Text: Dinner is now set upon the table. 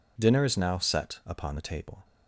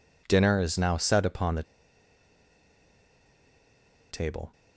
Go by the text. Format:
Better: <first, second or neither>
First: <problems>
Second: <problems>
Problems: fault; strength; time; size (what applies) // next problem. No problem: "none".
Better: first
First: none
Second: pauses between "the" and "table"; strong; at 1.6 s; 2.4 s long